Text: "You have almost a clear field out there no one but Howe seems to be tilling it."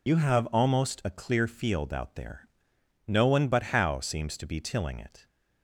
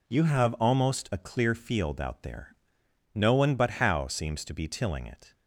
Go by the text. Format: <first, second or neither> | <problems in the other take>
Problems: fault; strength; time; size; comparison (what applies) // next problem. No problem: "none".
second | loses the start of "You"; at 0.0 s; 60 ms // pauses between "there" and "no"; noticeable; at 2.4 s; 0.62 s long; noticeable in the second